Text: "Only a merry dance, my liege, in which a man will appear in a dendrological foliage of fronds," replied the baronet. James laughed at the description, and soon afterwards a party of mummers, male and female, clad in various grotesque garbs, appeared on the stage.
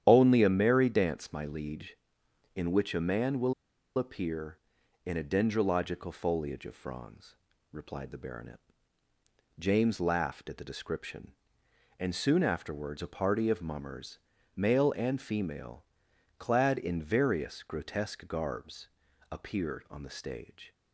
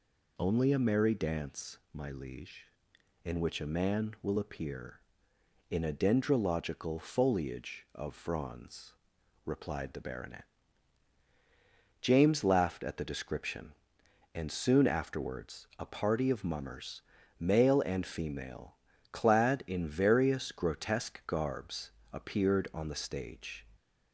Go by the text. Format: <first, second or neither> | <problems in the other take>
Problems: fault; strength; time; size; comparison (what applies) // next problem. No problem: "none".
second | starts louder than the rest; strong; until 1.0 s; 10 dB // pauses between "will" and "appear"; at 3.5 s; 0.44 s long